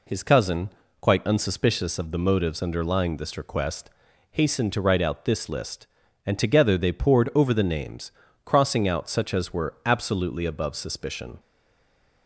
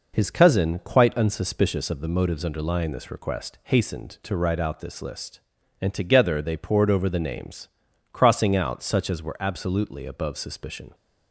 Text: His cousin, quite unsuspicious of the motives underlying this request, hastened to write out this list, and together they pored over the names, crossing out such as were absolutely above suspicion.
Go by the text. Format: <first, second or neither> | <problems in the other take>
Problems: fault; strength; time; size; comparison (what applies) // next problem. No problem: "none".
second | stays silent after the last word; slight; from 11.3 s on; 0.9 s long